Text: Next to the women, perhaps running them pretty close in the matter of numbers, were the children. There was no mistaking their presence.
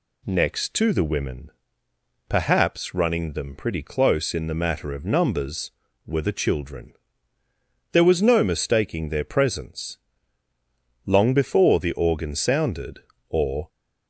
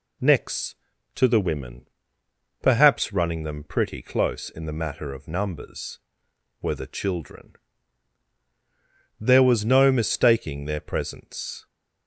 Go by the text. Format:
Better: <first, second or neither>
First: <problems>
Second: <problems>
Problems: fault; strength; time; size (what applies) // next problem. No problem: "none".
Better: second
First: goes on to say "Long before the organ sounded or"; strong; from 11.0 s on; 2.6 s long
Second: none